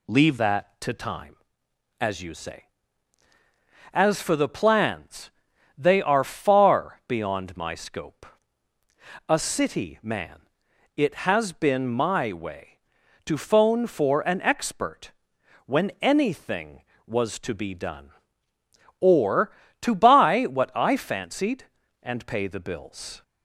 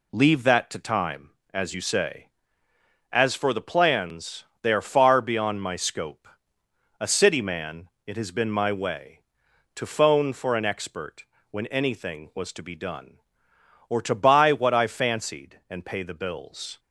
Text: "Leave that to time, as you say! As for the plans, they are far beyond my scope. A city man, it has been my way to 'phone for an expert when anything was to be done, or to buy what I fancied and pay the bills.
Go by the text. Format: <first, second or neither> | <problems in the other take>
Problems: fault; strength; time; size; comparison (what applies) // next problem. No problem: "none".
second | changes voice at "that"; from 0.3 s on; 22.9 s long // pauses between "expert" and "when"; noticeable; at 15.1 s; 0.56 s long; slight in the second